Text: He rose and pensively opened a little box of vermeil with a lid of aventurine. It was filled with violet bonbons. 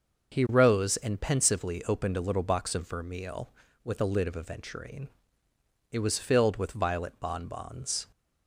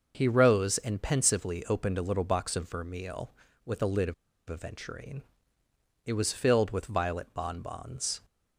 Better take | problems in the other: first | pauses between "of" and "aventurine"; slight; at 4.1 s; 0.34 s long

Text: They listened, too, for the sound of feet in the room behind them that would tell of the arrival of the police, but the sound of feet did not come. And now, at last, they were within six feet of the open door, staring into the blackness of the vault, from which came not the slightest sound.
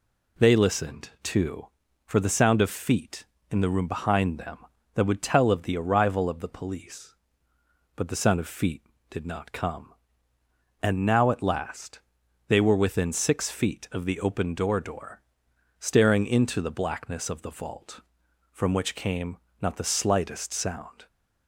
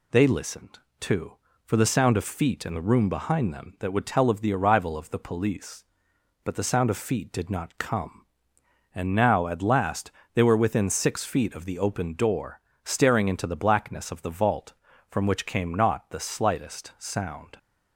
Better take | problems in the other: second | says "door" twice; at 14.7 s // pauses between "came" and "not"; slight; at 19.3 s; 0.22 s long

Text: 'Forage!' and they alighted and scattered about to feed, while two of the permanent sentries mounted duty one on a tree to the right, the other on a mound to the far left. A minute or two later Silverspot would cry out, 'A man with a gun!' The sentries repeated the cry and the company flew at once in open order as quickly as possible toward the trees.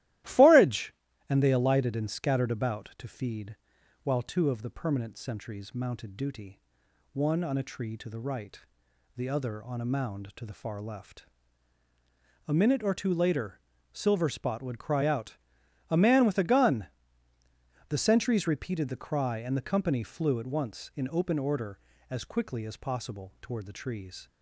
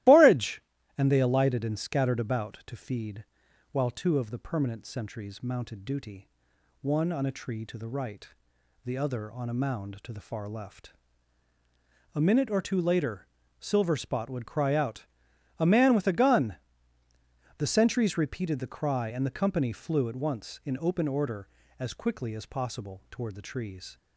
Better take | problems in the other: first | loses the start of "Forage"; at 0.0 s; 130 ms // starts louder than the rest; strong; until 1.4 s; 15.5 dB; strong in the first // pauses between "duty" and "one"; noticeable; at 6.2 s; 0.54 s long; noticeable in the first // pauses between "later" and "Silverspot"; slight; at 13.2 s; 0.34 s long; slight in the first

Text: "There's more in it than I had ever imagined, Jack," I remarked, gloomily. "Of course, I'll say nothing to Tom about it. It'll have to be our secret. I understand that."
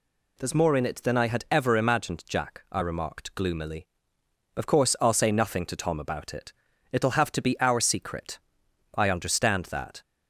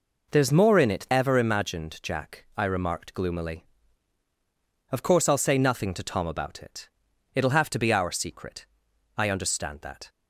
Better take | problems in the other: first | skips "than I had"; at 1.0 s

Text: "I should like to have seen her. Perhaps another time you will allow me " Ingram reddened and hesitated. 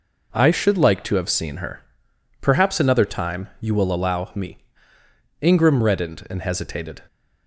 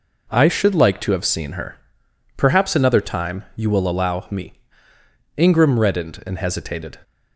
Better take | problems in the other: neither | none

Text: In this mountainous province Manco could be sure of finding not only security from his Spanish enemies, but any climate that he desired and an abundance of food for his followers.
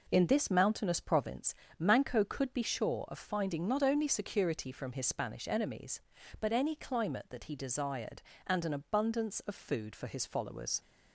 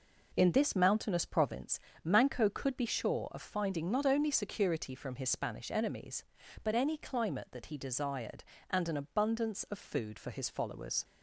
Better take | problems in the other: neither | pauses between "province" and "Manco"; slight; the same in both

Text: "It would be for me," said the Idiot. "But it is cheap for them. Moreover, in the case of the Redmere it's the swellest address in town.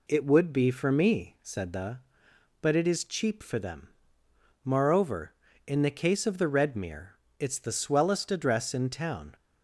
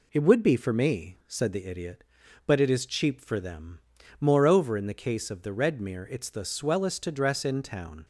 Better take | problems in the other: second | skips "Idiot"; at 2.2 s // pauses between "Redmere" and "it's"; slight; at 7.1 s; 0.24 s long

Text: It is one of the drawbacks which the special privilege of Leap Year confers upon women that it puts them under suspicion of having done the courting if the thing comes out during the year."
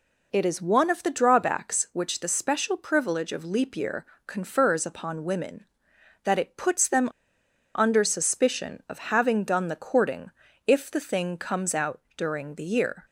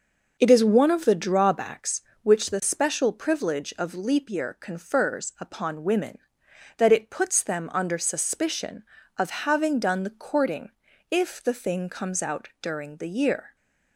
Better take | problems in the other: second | pauses between "Year" and "confers"; slight; at 4.0 s; 0.22 s long // pauses between "them" and "under"; noticeable; at 7.0 s; 0.67 s long // pauses between "courting" and "if"; slight; at 10.3 s; 0.36 s long; also in the second // pauses between "out" and "during"; slight; at 11.9 s; 0.18 s long

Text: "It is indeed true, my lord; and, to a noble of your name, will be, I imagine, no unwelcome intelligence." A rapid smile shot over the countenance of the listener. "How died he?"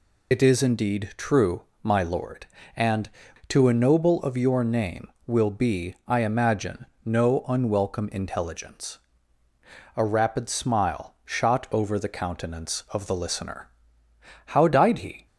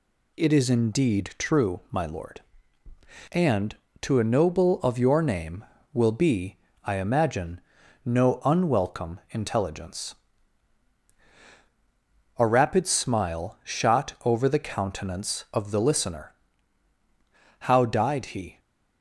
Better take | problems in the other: second | loses the start of "It"; at 0.3 s; 90 ms

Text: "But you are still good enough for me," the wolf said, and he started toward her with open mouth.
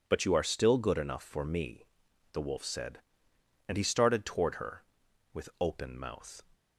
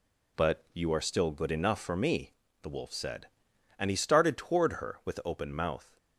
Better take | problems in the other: neither | none

